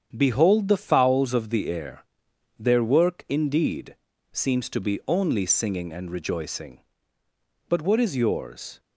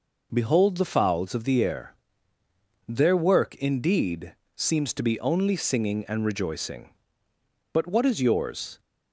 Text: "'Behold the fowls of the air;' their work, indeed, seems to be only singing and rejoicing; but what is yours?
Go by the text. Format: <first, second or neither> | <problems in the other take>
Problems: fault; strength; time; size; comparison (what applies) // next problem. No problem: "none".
second | gets quieter; noticeable; throughout; 6 dB